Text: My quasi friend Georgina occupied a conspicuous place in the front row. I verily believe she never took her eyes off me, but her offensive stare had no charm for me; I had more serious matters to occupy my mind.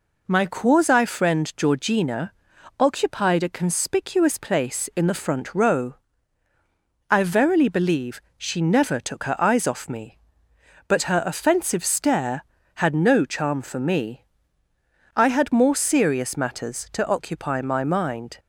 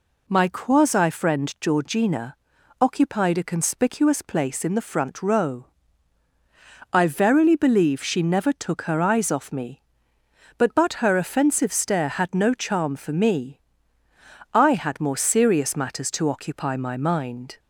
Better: first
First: pauses between "Georgina" and "occupied"; noticeable; at 2.3 s; 0.46 s long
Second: pauses between "Georgina" and "occupied"; noticeable; at 2.3 s; 0.46 s long // says "but" twice; at 10.7 s

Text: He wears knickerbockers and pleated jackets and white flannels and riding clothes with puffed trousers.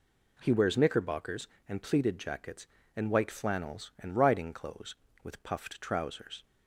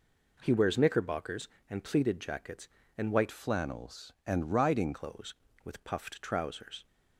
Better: first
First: none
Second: changes voice from "flannels" to "riding"; from 3.3 to 4.9 s; 1.6 s long

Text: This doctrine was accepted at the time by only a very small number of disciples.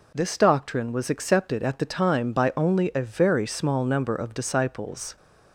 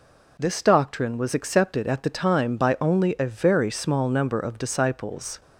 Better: neither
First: none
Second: none

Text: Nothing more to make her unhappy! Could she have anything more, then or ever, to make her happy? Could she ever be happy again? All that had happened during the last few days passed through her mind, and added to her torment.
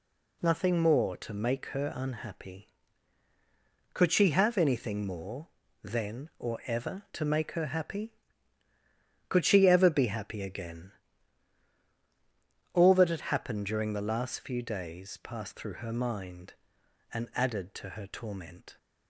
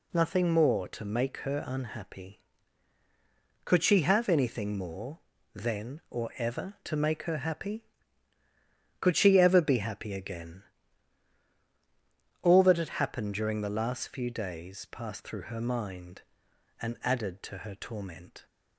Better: neither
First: none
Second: none

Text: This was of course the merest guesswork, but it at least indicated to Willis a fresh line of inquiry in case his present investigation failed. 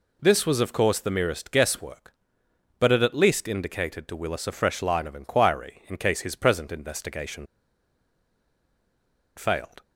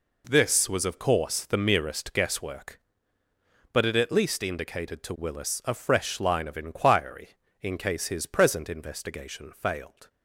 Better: second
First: pauses between "investigation" and "failed"; strong; at 7.4 s; 1.9 s long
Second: none

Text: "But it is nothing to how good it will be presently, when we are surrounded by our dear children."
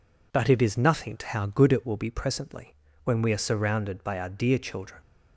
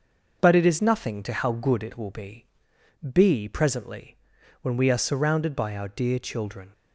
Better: first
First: none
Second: starts louder than the rest; noticeable; until 1.4 s; 6 dB // says "be" twice; at 3.1 s

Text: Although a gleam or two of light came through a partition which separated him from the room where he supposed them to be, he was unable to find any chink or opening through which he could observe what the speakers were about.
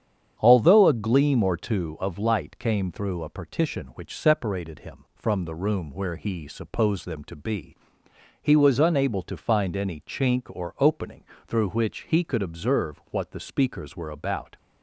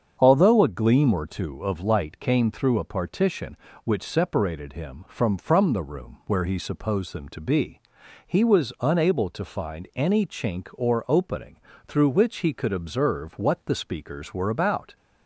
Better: first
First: starts louder than the rest; strong; until 1.4 s; 8.5 dB // pauses between "opening" and "through"; slight; at 11.2 s; 0.24 s long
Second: starts louder than the rest; strong; until 1.2 s; 7 dB // says "from" twice; at 5.3 s // pauses between "opening" and "through"; slight; at 11.5 s; 0.28 s long

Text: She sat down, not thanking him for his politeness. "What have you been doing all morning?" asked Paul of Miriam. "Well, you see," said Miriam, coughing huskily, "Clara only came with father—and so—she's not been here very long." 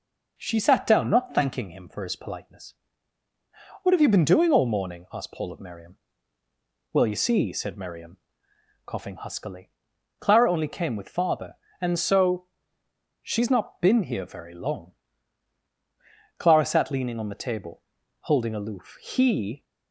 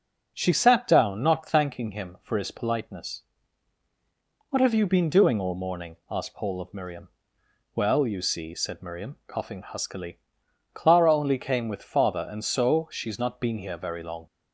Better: second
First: goes on to say "Clara sat leaning on the table holding aloof He"; strong; from 16.3 s on; 3.2 s long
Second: none

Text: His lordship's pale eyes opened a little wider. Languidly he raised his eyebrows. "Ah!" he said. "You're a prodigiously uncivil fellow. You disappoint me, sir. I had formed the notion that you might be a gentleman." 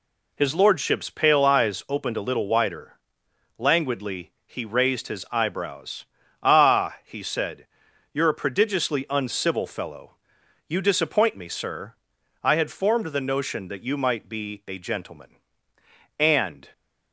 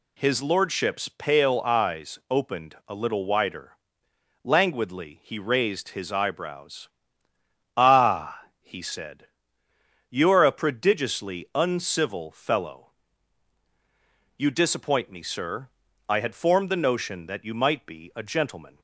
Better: second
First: pauses between "Languidly" and "he"; slight; at 4.3 s; 0.16 s long // goes on to say "And"; from 16.1 s on; 0.52 s long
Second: none

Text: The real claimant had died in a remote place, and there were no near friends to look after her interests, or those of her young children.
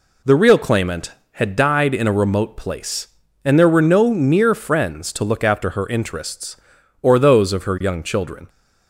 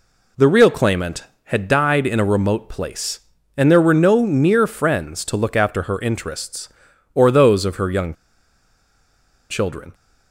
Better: first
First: none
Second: pauses between "young" and "children"; strong; at 8.1 s; 1.3 s long

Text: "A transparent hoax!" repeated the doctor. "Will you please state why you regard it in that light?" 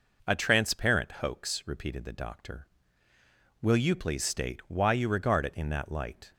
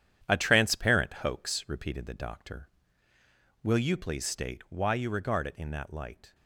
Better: first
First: none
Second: gets quieter; throughout; 7 dB

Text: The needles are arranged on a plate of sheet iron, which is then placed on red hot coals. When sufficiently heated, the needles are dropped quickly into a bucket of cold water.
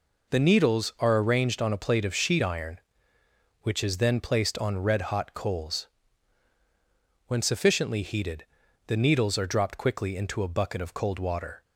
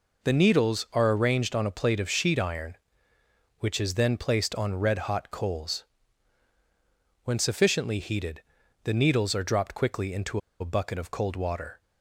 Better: first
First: none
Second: pauses between "into" and "a"; slight; at 10.3 s; 0.21 s long

